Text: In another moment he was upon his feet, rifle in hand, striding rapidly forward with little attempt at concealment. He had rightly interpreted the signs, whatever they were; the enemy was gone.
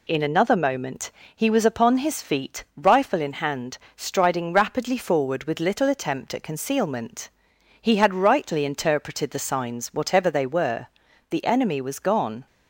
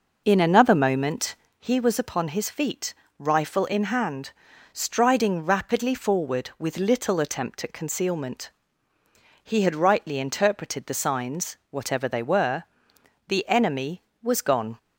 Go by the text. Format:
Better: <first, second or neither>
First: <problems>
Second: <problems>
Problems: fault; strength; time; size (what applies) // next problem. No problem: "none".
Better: first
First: pauses between "moment" and "he"; slight; at 1.1 s; 0.24 s long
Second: starts louder than the rest; noticeable; until 1.8 s; 5.5 dB // pauses between "moment" and "he"; slight; at 1.3 s; 0.24 s long